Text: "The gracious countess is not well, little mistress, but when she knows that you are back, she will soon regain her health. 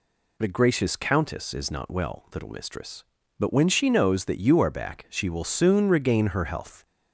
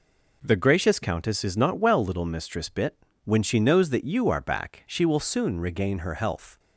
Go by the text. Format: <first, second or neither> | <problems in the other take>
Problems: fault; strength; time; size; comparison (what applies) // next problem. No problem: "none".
first | says "bit" for "but"; at 2.6 s